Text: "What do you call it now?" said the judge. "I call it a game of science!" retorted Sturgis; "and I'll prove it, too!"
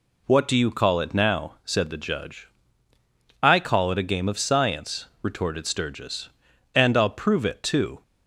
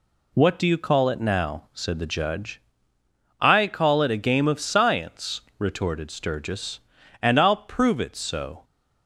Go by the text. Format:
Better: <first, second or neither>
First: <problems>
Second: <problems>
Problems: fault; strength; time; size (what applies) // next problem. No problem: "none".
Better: first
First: none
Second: says "so" for "too"; at 8.1 s